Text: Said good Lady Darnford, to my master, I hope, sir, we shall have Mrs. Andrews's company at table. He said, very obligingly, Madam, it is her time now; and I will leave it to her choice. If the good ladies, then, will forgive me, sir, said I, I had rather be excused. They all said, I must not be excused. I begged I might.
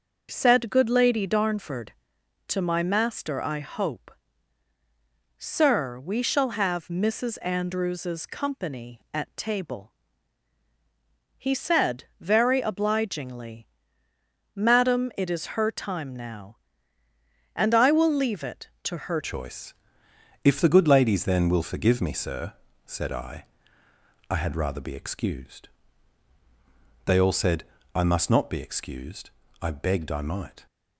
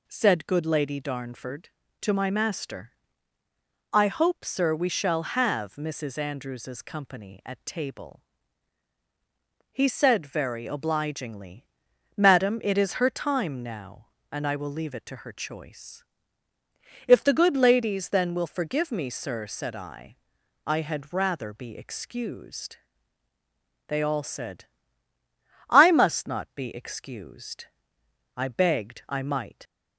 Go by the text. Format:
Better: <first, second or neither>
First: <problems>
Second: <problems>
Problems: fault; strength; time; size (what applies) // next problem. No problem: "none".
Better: second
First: starts louder than the rest; until 1.3 s; 6.5 dB // changes voice at "choice"; from 19.2 s on; 11.4 s long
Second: none